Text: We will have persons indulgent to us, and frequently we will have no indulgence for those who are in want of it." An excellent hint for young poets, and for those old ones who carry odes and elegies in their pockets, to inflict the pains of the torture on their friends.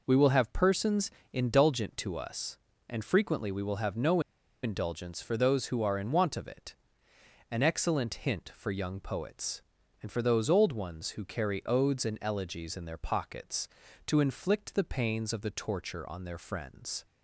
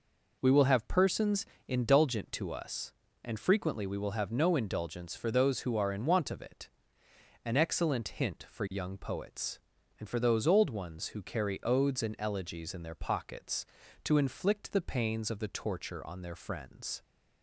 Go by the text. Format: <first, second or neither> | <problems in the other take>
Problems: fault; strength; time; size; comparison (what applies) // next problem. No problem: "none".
second | pauses between "persons" and "indulgent"; slight; at 1.0 s; 0.22 s long; slight in the second // pauses between "no" and "indulgence"; at 4.1 s; 0.43 s long